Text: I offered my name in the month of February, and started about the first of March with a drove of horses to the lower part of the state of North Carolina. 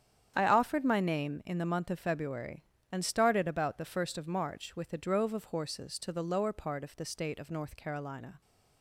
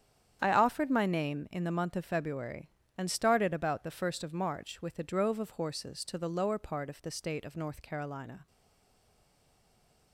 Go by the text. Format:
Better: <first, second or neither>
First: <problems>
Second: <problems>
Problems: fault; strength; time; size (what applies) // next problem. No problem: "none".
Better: first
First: starts louder than the rest; strong; until 1.3 s; 9 dB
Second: starts louder than the rest; strong; until 1.4 s; 9 dB // stays silent after the last word; noticeable; from 8.4 s on; 1.7 s long